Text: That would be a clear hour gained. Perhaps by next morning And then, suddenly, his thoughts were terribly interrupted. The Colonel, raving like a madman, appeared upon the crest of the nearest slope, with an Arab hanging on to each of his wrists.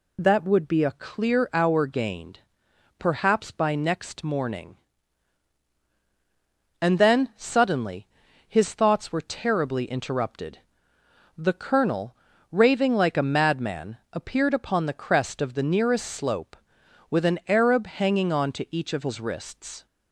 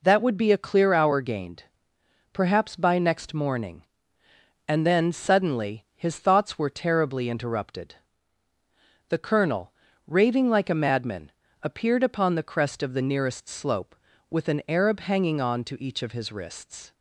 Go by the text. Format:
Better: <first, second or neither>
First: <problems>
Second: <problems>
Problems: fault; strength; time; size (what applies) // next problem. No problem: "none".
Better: neither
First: none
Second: none